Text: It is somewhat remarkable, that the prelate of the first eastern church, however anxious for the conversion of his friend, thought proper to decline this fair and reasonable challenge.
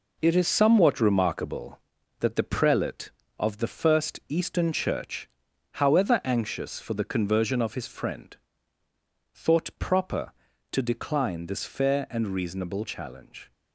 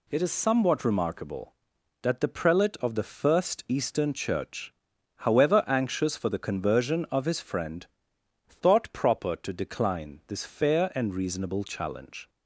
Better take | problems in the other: second | gets quieter; throughout; 6.5 dB

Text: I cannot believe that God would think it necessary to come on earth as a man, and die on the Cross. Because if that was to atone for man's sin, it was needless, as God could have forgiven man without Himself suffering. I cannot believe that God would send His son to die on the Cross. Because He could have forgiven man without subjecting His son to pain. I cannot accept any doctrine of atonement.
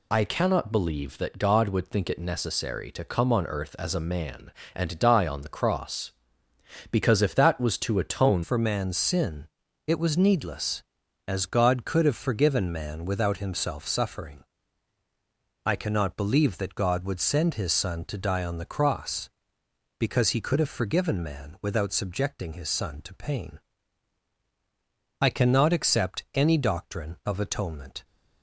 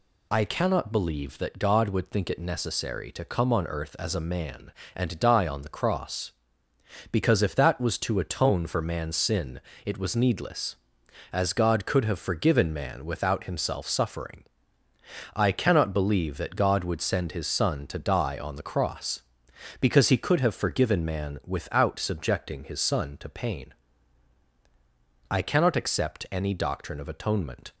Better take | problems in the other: second | changes voice at "for"; from 8.4 s on; 19.6 s long

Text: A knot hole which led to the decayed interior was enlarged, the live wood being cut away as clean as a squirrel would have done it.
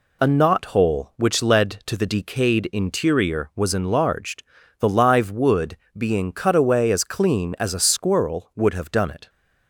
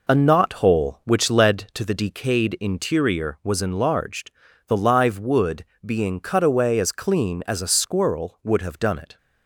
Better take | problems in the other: first | starts louder than the rest; noticeable; until 1.6 s; 4 dB // pauses between "wood" and "being"; slight; at 5.6 s; 0.20 s long; slight in the first

